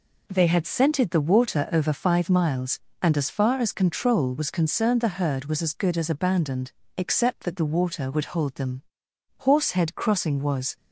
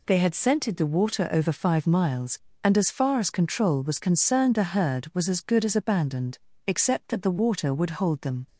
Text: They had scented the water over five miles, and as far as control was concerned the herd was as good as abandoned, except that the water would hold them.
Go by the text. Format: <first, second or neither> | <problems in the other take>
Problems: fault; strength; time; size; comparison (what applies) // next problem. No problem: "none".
second | goes on to say "Horsehead Crossing was"; from 9.3 s on; 1.3 s long